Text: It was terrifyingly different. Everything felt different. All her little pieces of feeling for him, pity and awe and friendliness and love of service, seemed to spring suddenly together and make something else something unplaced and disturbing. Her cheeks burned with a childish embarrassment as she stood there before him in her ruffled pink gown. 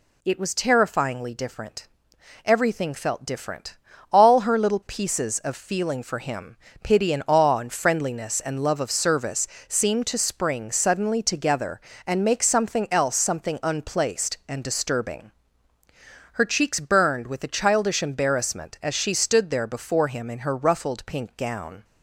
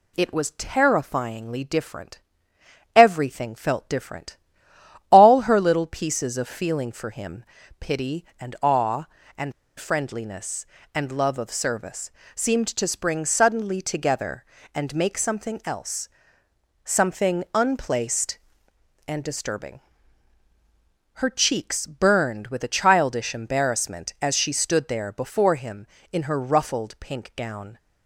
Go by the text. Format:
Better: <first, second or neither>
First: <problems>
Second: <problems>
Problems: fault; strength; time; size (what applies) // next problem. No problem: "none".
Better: first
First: none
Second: pauses between "and" and "friendliness"; slight; at 9.5 s; 0.27 s long // pauses between "else" and "something"; noticeable; at 16.0 s; 0.76 s long